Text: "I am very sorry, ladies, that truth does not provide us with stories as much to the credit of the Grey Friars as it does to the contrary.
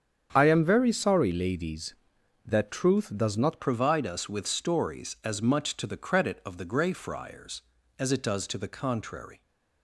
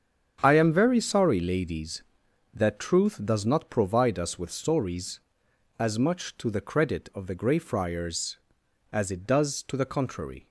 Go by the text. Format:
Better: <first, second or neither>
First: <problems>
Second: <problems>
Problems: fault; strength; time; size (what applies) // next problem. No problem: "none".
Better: second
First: starts louder than the rest; strong; until 1.3 s; 8 dB // changes voice at "provide"; from 3.5 s on; 5.9 s long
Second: starts louder than the rest; strong; until 1.4 s; 8 dB